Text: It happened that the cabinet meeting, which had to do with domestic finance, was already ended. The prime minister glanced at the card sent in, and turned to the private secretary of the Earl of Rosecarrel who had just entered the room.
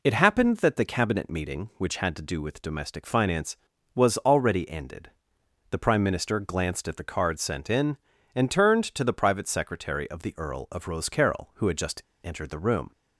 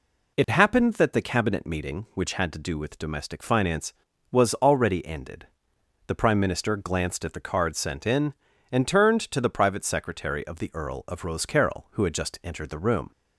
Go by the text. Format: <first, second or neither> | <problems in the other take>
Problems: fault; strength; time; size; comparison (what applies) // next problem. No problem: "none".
second | pauses between "just" and "entered"; slight; at 12.0 s; 0.22 s long